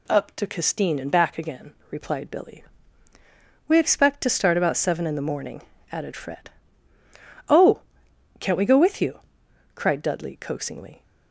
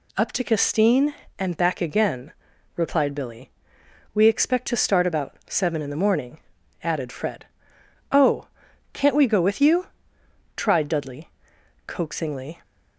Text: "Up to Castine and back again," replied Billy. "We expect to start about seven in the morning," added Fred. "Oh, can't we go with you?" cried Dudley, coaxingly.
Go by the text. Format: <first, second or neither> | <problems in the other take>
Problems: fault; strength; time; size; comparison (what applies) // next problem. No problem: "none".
first | says "tried" for "cried"; at 10.5 s